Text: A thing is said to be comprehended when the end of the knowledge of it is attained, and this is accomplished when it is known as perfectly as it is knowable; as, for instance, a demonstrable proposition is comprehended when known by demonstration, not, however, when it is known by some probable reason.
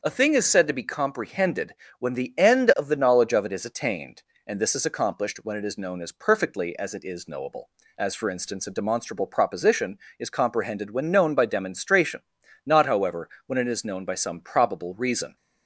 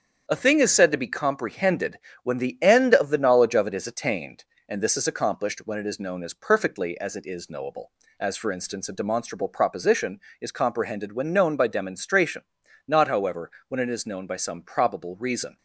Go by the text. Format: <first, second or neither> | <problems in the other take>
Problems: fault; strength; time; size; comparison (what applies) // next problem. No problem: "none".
first | gets quieter; noticeable; throughout; 5 dB // starts louder than the rest; strong; until 1.3 s; 8 dB; also in the first // pauses between "comprehended" and "when"; slight; at 1.9 s; 0.24 s long; slight in the first